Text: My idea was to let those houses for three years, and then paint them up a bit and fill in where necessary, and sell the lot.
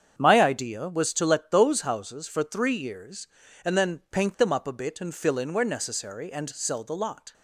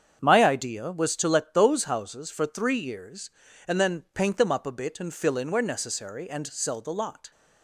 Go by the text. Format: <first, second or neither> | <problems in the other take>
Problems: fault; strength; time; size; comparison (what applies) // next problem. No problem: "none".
neither | starts louder than the rest; strong; the same in both